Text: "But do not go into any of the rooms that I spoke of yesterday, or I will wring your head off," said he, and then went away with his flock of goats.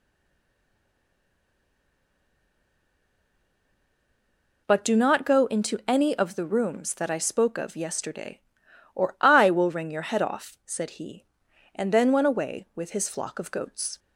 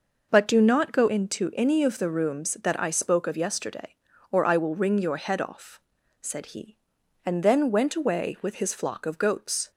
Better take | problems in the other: second | stays silent before the first word; strong; until 4.6 s; 4.6 s long

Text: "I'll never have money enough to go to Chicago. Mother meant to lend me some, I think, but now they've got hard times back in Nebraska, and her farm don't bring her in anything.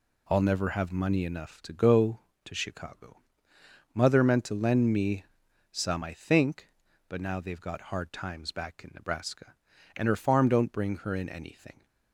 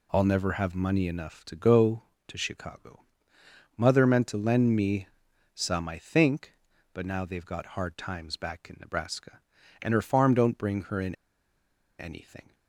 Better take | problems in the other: first | pauses between "me" and "some"; noticeable; at 5.0 s; 0.48 s long; noticeable in the first // pauses between "in" and "anything"; noticeable; at 11.1 s; 0.84 s long

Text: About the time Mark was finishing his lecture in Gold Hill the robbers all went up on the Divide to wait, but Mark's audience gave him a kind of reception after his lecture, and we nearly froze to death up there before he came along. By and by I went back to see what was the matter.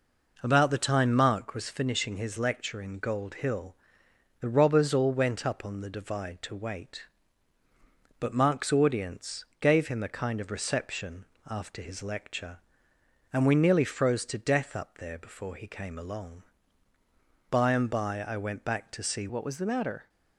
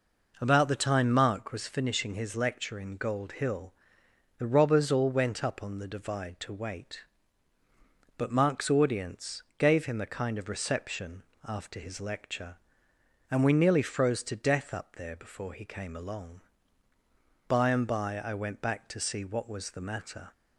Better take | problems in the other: second | pauses between "Hill" and "the"; noticeable; at 3.7 s; 0.64 s long; noticeable in the second // pauses between "audience" and "gave"; slight; at 9.4 s; 0.16 s long; slight in the second // pauses between "reception" and "after"; slight; at 11.2 s; 0.24 s long; slight in the second // changes voice at "what"; from 19.2 s on; 0.8 s long

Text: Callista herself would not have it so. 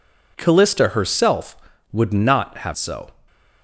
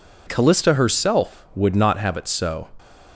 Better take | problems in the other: second | skips "it"; at 2.7 s

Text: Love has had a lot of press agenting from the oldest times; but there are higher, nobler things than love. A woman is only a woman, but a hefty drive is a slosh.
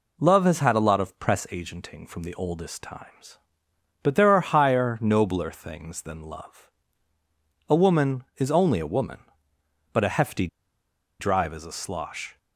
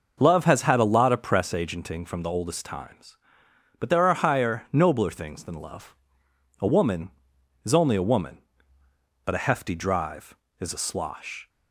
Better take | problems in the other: second | pauses between "hefty" and "drive"; noticeable; at 10.4 s; 0.72 s long

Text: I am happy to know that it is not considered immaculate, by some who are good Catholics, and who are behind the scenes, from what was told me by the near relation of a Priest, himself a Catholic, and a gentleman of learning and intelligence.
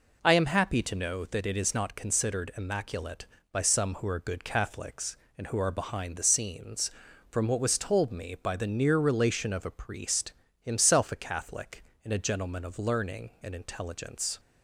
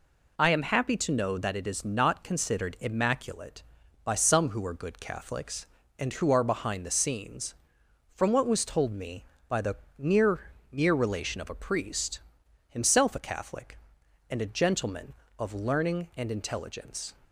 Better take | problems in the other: first | pauses between "the" and "near"; slight; at 9.7 s; 0.20 s long // says "near" twice; at 10.7 s

